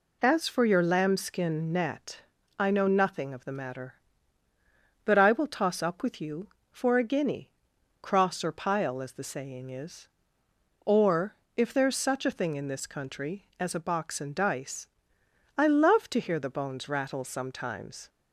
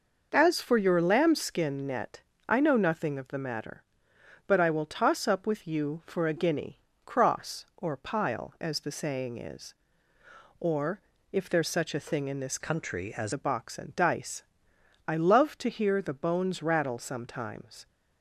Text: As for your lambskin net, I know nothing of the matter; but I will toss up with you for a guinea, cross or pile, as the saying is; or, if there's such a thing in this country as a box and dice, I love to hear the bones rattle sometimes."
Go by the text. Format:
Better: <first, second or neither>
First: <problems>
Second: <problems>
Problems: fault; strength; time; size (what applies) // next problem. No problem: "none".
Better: first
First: none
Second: changes voice from "country" to "as"; from 12.6 to 13.3 s; 0.7 s long